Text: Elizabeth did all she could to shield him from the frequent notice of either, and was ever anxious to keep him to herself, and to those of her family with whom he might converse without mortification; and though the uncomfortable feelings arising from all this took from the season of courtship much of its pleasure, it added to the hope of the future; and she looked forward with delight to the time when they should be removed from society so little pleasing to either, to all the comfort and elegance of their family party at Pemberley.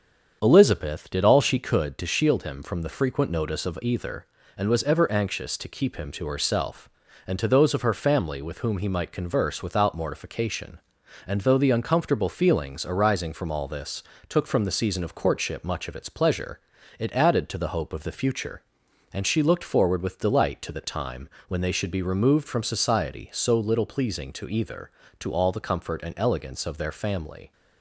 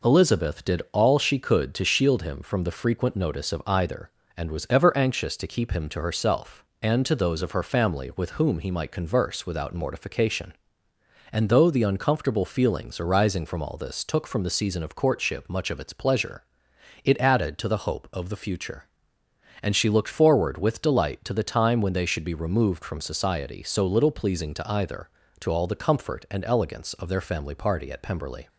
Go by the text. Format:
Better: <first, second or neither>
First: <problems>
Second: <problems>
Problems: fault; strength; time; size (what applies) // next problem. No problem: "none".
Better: second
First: starts louder than the rest; strong; until 1.4 s; 7.5 dB // pauses between "this" and "took"; slight; at 14.0 s; 0.26 s long // pauses between "time" and "when"; slight; at 21.2 s; 0.18 s long // stops before "party at Pemberley"; at 27.5 s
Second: none